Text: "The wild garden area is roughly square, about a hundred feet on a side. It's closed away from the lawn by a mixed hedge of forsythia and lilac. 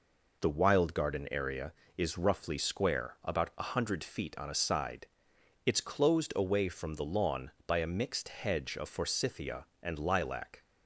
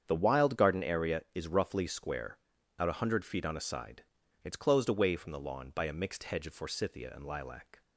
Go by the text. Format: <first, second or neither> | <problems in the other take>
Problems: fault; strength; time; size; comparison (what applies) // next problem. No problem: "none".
first | starts louder than the rest; strong; until 1.0 s; 8 dB // says "out" for "about"; at 2.7 s